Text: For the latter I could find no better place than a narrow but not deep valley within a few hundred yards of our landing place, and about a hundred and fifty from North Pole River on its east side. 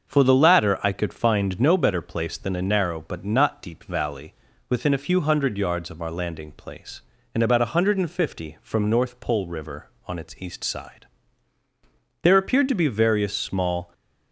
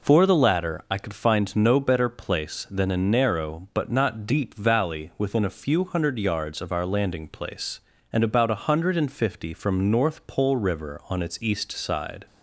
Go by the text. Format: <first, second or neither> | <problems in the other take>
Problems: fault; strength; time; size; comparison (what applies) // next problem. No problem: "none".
second | starts louder than the rest; until 1.1 s; 6.5 dB // pauses between "valley" and "within"; at 4.3 s; 0.38 s long // goes on to say "There appeared to be various small"; strong; from 12.2 s on; 1.7 s long